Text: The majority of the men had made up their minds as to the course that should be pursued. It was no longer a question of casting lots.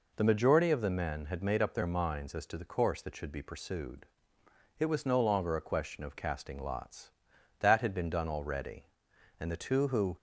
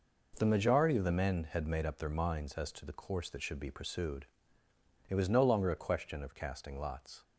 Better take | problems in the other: second | goes on to say "That had been done already and the two who"; strong; from 7.5 s on; 2.5 s long

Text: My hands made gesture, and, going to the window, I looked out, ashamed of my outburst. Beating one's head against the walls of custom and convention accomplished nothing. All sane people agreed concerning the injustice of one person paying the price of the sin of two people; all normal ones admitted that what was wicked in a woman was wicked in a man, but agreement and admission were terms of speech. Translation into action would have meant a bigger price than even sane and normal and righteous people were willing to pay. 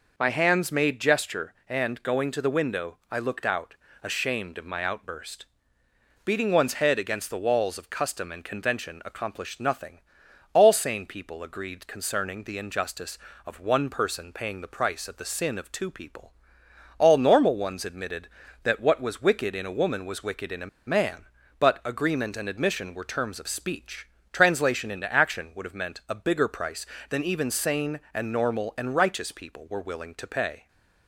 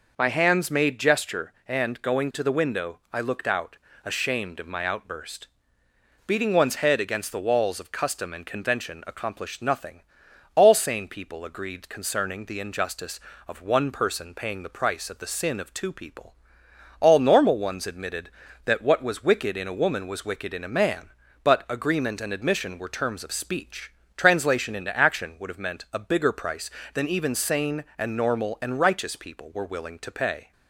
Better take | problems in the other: second | pauses between "a" and "man"; slight; at 20.6 s; 0.20 s long

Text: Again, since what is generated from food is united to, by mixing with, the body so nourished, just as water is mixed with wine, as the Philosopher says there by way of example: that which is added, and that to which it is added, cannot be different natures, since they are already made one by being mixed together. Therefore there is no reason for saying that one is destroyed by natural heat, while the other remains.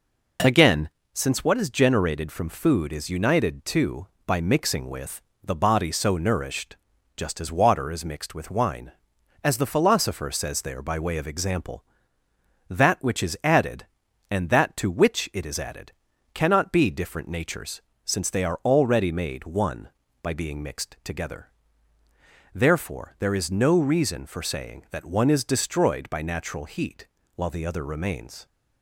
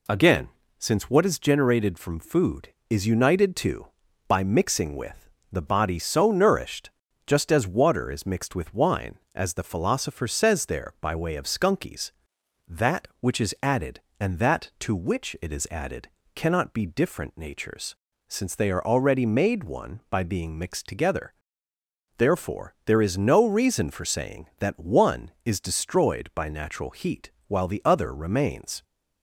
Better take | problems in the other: first | says "skunkies" for "example"; at 11.4 s

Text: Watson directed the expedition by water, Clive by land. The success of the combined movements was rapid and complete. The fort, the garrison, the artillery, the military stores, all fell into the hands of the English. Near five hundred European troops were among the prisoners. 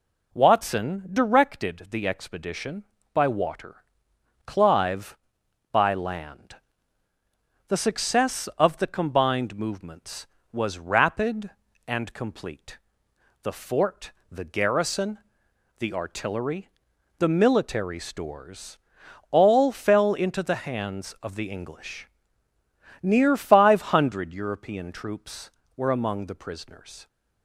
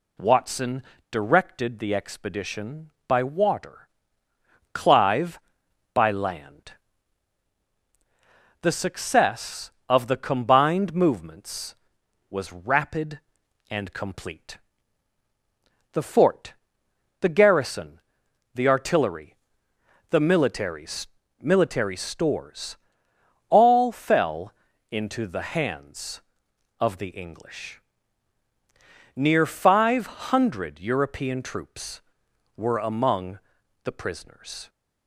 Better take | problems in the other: first | pauses between "Watson" and "directed"; slight; at 0.8 s; 0.28 s long // says "military" twice; at 21.3 s // pauses between "fell" and "into"; at 24.5 s; 0.38 s long // pauses between "among" and "the"; noticeable; at 33.3 s; 0.46 s long

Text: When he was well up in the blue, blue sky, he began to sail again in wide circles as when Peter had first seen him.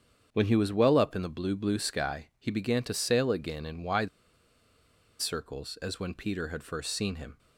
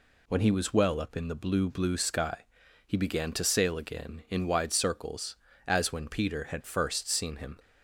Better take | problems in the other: second | starts louder than the rest; strong; until 1.3 s; 7.5 dB // pauses between "wide" and "circles"; at 4.0 s; 1.1 s long

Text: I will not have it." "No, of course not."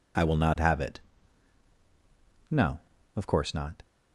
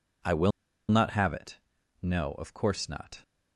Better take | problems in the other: first | pauses between "will" and "not"; at 0.5 s; 0.39 s long

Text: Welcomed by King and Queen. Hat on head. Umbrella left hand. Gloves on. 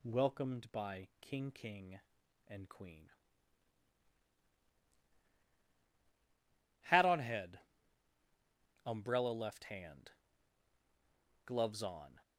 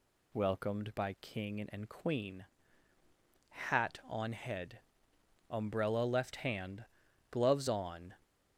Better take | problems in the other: second | says "King" twice; at 1.5 s

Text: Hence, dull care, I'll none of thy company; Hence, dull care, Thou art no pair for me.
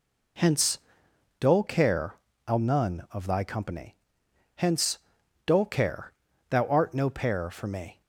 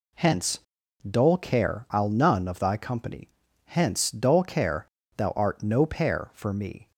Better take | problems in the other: neither | none

